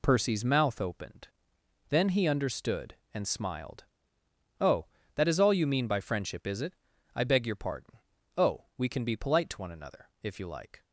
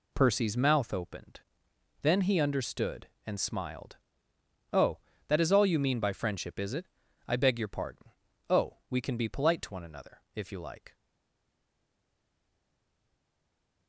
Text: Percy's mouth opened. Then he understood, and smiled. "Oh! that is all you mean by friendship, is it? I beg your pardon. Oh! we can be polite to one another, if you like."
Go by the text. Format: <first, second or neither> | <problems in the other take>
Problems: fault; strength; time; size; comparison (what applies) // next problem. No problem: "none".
first | stays silent after the last word; strong; from 10.9 s on; 2.9 s long